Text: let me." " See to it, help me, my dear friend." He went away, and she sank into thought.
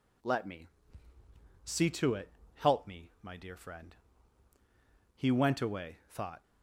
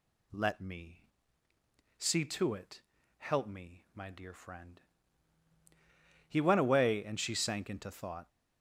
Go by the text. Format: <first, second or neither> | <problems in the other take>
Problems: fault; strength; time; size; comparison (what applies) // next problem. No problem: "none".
second | skips "and she sank into"; at 6.0 s